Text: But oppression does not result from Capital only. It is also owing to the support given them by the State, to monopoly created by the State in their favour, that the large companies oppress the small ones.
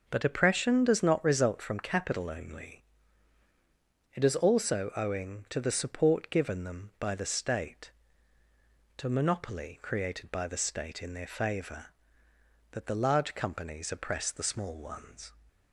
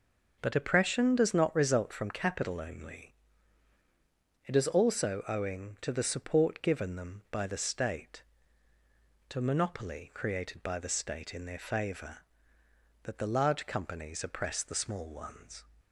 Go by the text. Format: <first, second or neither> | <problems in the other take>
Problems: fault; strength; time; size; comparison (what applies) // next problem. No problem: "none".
neither | none